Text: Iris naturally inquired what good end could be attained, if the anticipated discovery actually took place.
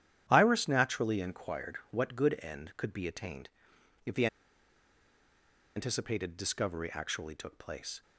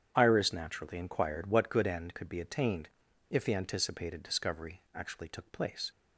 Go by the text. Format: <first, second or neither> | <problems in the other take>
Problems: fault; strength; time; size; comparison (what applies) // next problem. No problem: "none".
second | starts louder than the rest; strong; until 1.2 s; 10.5 dB; strong in the second // pauses between "the" and "anticipated"; strong; at 4.2 s; 1.4 s long